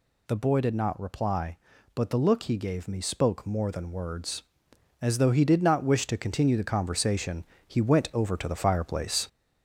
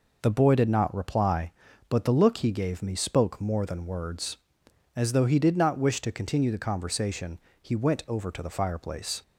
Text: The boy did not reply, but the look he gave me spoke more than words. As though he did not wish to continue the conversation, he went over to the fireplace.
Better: second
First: gets louder; noticeable; throughout; 4 dB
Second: none

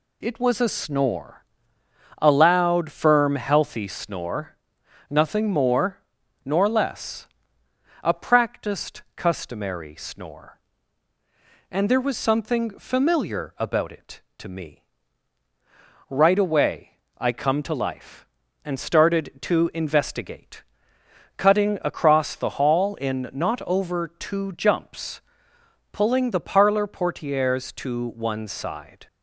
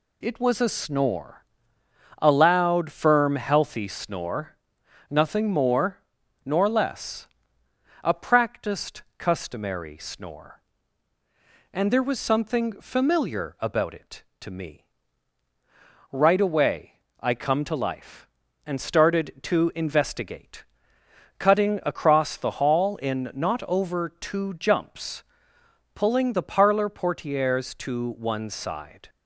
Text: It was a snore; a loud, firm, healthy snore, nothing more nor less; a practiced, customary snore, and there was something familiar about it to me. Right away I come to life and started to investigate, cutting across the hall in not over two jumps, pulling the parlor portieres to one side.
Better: neither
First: pauses between "more" and "nor"; noticeable; at 5.9 s; 0.48 s long // pauses between "away" and "I"; slight; at 16.9 s; 0.18 s long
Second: pauses between "more" and "nor"; noticeable; at 5.9 s; 0.48 s long // pauses between "away" and "I"; slight; at 16.9 s; 0.18 s long

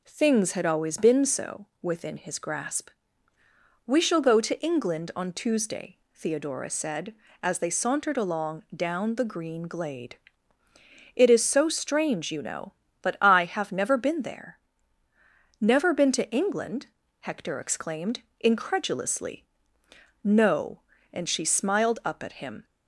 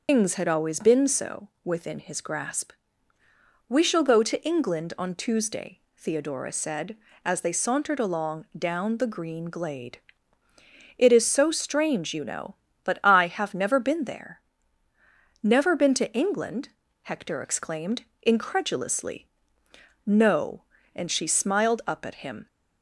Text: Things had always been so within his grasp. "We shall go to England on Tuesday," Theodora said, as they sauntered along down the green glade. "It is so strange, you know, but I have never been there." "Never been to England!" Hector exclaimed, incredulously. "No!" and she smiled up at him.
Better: first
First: none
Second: loses the start of "Things"; at 0.0 s; 220 ms // starts louder than the rest; until 1.0 s; 6 dB

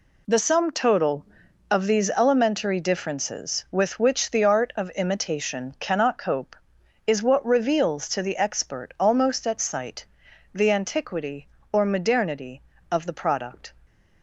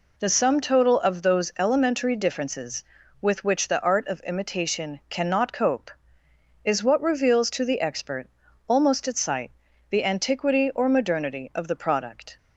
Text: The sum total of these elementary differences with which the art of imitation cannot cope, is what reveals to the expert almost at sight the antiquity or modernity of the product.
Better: first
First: pauses between "sight" and "the"; noticeable; at 10.0 s; 0.48 s long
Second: says "those" for "these"; at 1.2 s // pauses between "expert" and "almost"; at 8.2 s; 0.40 s long // pauses between "sight" and "the"; at 9.5 s; 0.38 s long

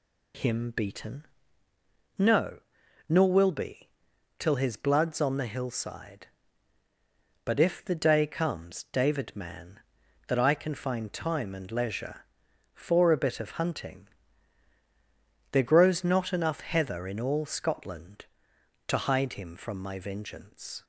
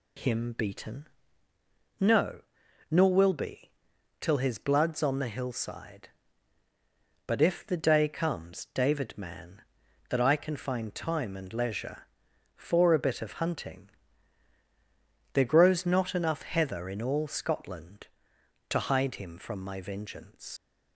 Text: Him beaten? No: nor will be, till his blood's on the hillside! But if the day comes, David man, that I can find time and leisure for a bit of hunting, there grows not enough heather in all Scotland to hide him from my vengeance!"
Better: first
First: none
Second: leaves "vengeance" unfinished; at 20.5 s; 90 ms

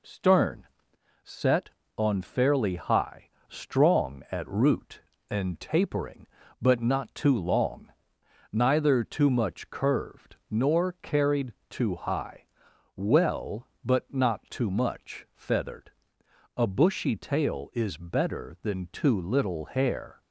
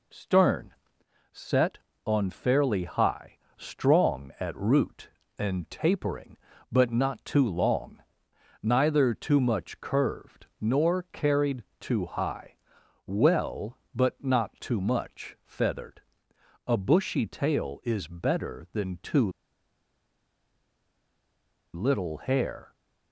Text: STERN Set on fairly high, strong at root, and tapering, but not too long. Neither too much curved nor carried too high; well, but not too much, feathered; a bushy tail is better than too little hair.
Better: first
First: pauses between "STERN" and "Set"; noticeable; at 0.6 s; 0.56 s long // pauses between "carried" and "too"; slight; at 11.5 s; 0.18 s long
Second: pauses between "STERN" and "Set"; noticeable; at 0.7 s; 0.58 s long // pauses between "carried" and "too"; slight; at 11.6 s; 0.18 s long // pauses between "too" and "little"; strong; at 19.2 s; 2.4 s long

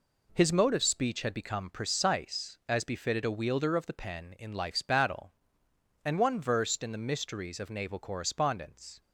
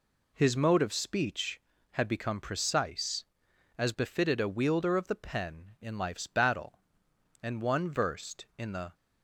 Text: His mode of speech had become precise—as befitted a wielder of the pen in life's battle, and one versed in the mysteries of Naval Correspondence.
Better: first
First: none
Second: stops before "mysteries of Naval Correspondence"; at 8.9 s

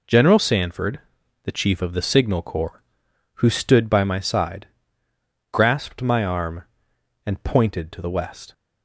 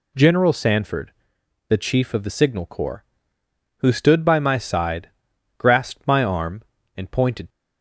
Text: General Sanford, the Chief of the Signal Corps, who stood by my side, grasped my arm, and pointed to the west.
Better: first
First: none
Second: stops before "to the west"; at 7.5 s

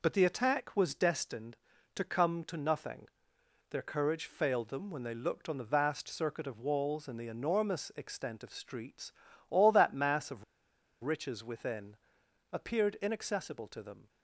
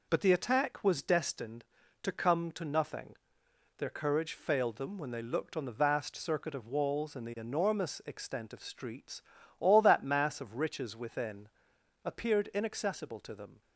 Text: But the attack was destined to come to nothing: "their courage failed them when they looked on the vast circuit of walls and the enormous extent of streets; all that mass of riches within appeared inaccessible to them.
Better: second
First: pauses between "of" and "riches"; noticeable; at 10.4 s; 0.60 s long // pauses between "within" and "appeared"; noticeable; at 11.9 s; 0.56 s long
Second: pauses between "within" and "appeared"; noticeable; at 11.4 s; 0.56 s long

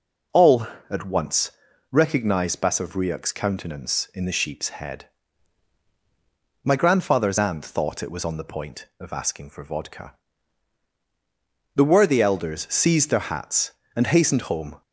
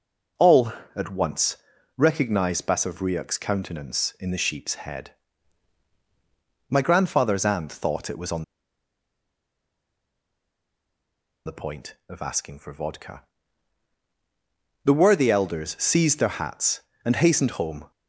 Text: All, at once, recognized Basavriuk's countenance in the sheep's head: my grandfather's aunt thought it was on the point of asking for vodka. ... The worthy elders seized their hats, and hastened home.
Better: first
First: none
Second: pauses between "on" and "the"; strong; at 8.4 s; 3.0 s long

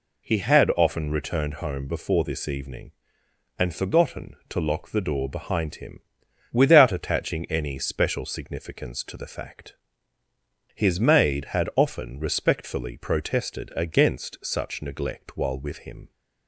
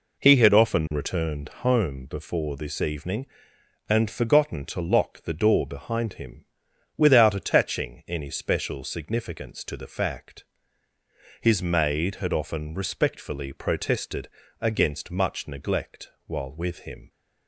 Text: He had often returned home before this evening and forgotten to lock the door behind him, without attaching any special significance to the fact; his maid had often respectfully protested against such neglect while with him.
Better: first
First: none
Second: pauses between "protested" and "against"; slight; at 14.2 s; 0.32 s long // says "much" for "such"; at 15.0 s // pauses between "neglect" and "while"; slight; at 16.1 s; 0.16 s long

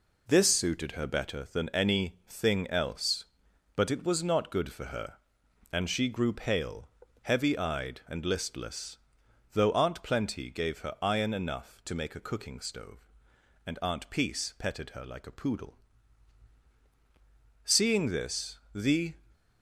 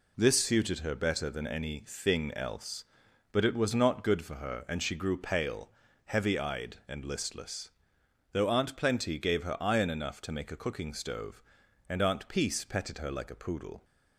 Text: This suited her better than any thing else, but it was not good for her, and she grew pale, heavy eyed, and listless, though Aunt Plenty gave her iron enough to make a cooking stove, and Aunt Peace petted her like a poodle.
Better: second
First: goes on to say "Seeing this the"; from 17.6 s on; 1.5 s long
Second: none

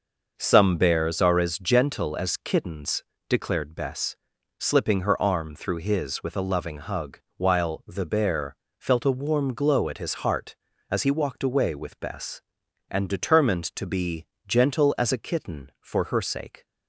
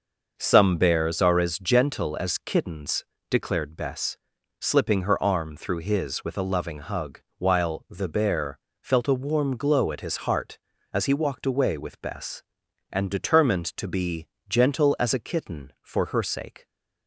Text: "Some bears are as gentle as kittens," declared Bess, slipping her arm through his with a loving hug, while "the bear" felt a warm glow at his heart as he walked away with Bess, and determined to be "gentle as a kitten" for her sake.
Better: neither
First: starts louder than the rest; noticeable; until 1.3 s; 6 dB // pauses between "bear" and "felt"; slight; at 8.5 s; 0.24 s long // pauses between "be" and "gentle"; slight; at 14.2 s; 0.22 s long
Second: starts louder than the rest; noticeable; until 1.3 s; 6 dB // pauses between "bear" and "felt"; slight; at 8.5 s; 0.24 s long // pauses between "be" and "gentle"; slight; at 14.2 s; 0.22 s long

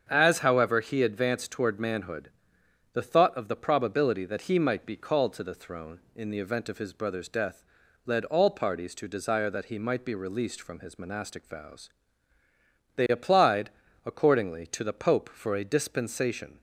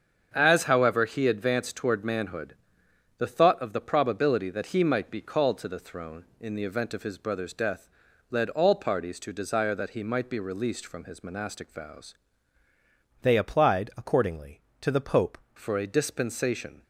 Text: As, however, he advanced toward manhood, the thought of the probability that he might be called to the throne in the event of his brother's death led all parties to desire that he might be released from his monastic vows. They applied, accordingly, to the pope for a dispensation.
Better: first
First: starts louder than the rest; strong; until 1.1 s; 7.5 dB // pauses between "death" and "led"; at 7.6 s; 0.44 s long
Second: starts louder than the rest; strong; until 1.3 s; 7.5 dB // pauses between "death" and "led"; at 7.8 s; 0.44 s long // changes voice from "They" to "pope"; from 13.2 to 15.3 s; 2.1 s long

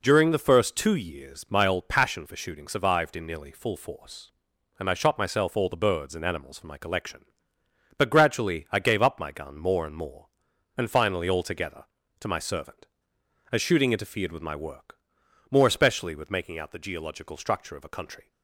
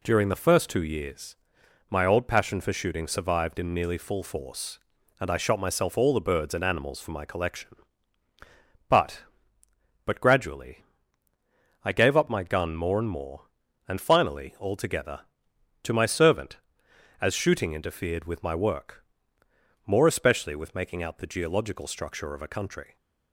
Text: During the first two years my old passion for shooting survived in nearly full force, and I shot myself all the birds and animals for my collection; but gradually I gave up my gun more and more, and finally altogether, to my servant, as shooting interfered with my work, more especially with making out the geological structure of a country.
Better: first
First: none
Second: pauses between "years" and "my"; noticeable; at 1.3 s; 0.52 s long // says "but" twice; at 10.0 s // pauses between "gradually" and "I"; at 10.8 s; 1.0 s long

